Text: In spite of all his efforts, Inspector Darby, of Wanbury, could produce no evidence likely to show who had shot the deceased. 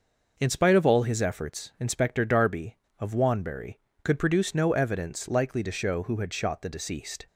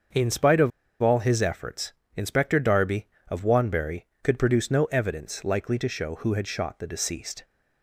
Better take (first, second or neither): first